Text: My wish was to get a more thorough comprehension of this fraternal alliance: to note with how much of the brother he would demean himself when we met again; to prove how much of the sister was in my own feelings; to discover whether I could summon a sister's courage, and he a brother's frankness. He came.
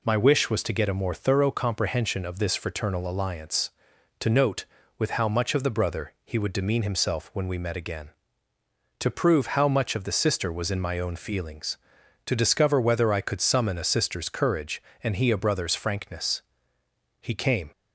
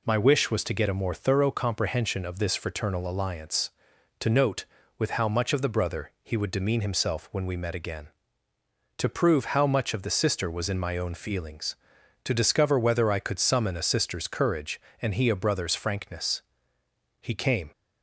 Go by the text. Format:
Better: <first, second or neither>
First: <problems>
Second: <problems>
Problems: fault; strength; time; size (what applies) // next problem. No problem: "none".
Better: neither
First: none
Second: none